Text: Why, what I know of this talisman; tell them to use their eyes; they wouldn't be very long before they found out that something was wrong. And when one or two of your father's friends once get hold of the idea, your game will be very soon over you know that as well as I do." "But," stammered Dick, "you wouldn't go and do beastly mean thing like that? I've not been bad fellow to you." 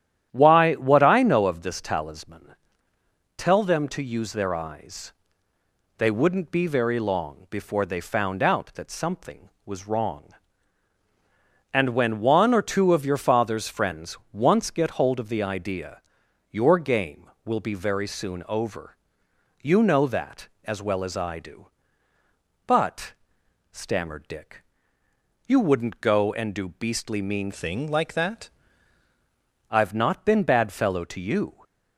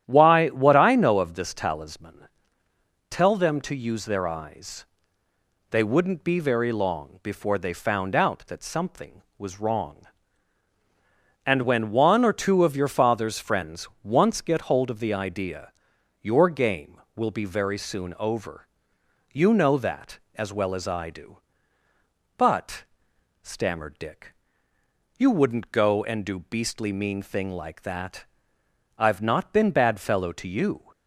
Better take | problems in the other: second | starts louder than the rest; strong; until 1.3 s; 11 dB; strong in the second // pauses between "over" and "you"; noticeable; at 18.9 s; 0.64 s long; noticeable in the second // changes voice from "thing" to "that"; from 27.5 to 28.4 s; 0.9 s long

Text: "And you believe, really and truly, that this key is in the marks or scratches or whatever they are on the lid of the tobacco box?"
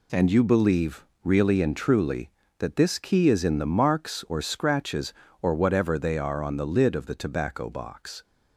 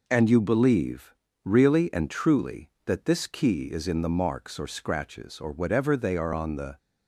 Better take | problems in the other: first | stops before "lid of the tobacco box"; at 6.7 s

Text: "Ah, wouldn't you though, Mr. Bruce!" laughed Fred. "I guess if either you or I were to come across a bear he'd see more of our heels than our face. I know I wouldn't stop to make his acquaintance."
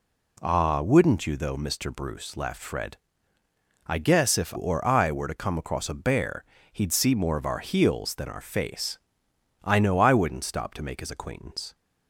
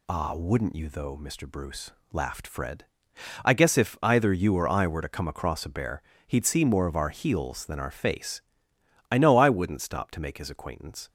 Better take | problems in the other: second | skips "either you"; at 4.5 s // pauses between "bear" and "he'd"; slight; at 6.4 s; 0.26 s long; slight in the second

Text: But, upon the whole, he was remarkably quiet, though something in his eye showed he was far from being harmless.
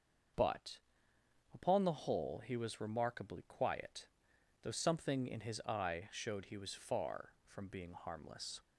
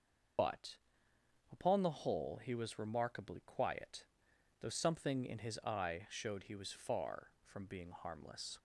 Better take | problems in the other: first | loses the start of "But"; at 0.3 s; 45 ms // starts louder than the rest; until 2.1 s; 6 dB; also in the first

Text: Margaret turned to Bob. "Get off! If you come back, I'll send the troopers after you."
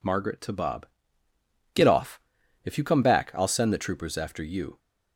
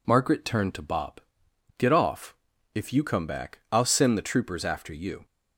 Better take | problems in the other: second | skips "turned"; at 0.4 s

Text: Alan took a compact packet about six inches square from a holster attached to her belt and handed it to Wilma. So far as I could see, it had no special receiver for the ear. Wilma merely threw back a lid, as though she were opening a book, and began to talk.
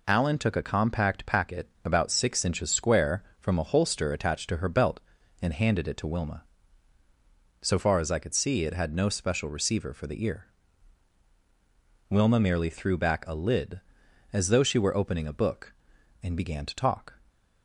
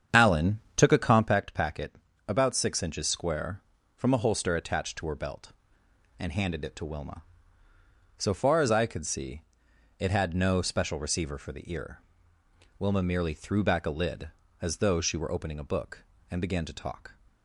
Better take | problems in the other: first | starts louder than the rest; strong; until 1.4 s; 8 dB // pauses between "Alan" and "took"; slight; at 0.5 s; 0.16 s long // pauses between "packet" and "about"; slight; at 1.9 s; 0.32 s long; slight in the first

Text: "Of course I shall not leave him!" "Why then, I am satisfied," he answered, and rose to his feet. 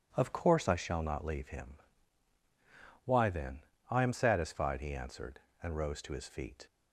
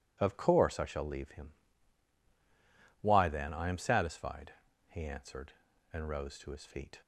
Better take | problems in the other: first | skips "not"; at 1.0 s

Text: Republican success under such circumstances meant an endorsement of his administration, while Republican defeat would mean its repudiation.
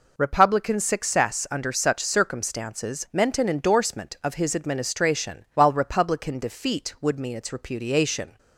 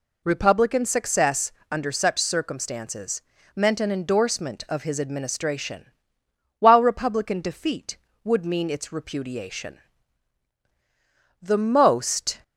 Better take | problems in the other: first | pauses between "success" and "under"; slight; at 1.5 s; 0.18 s long // pauses between "circumstances" and "meant"; slight; at 3.2 s; 0.34 s long // goes on to say "The most"; noticeable; from 11.4 s on; 1.0 s long

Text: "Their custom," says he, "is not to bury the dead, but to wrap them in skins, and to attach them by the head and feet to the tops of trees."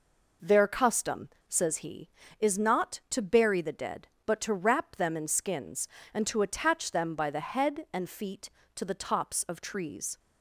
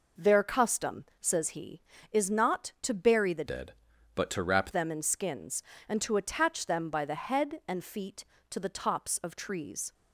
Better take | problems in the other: first | changes voice from "dead" to "wrap"; from 3.4 to 4.7 s; 1.3 s long

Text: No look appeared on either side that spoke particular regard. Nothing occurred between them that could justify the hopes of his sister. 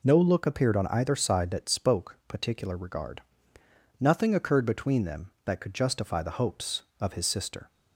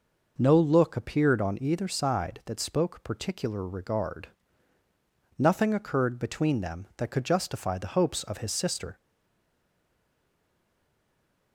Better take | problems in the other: first | stays silent after the last word; strong; from 8.9 s on; 2.6 s long

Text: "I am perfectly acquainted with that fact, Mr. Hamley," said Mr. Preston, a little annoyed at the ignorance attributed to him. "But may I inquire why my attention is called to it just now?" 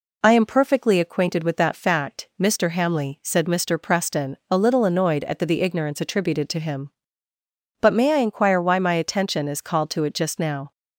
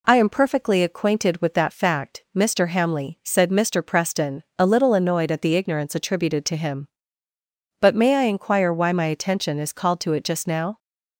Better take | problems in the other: second | says "the" twice; at 5.4 s

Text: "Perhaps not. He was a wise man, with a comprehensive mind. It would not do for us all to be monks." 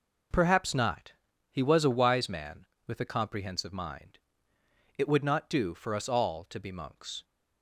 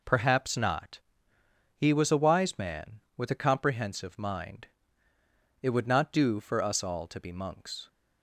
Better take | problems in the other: neither | none

